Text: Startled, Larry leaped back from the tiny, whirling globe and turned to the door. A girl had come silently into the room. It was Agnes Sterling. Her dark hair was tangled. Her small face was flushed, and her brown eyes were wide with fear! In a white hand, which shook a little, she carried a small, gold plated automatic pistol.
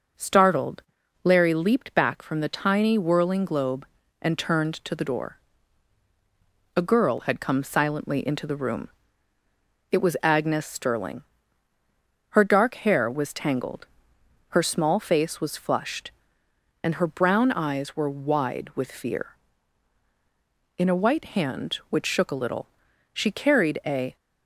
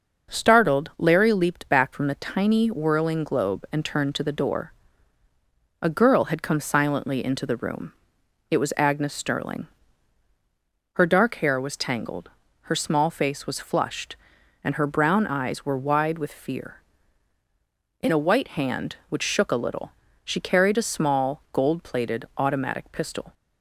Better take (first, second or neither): second